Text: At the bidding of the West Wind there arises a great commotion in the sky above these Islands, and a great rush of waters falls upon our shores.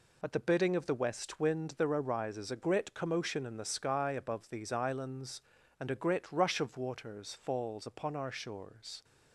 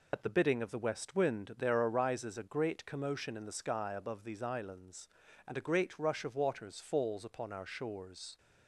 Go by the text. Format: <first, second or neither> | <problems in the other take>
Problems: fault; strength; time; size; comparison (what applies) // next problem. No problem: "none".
first | loses the start of "At"; at 0.1 s; 65 ms